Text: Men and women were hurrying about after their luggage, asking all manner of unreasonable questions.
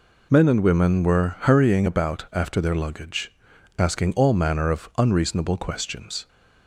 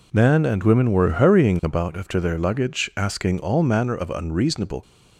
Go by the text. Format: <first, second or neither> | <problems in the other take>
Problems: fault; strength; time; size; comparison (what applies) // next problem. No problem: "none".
first | stops before "questions"; at 4.8 s